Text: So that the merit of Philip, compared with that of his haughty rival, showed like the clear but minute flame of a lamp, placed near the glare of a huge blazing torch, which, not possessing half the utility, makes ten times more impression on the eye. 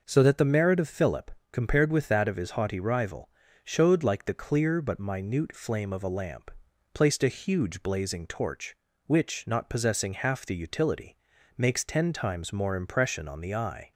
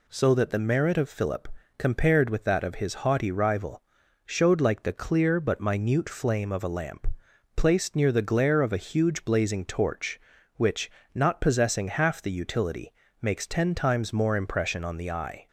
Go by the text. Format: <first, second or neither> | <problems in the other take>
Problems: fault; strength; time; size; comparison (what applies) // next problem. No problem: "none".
second | skips "near the glare of"; at 7.2 s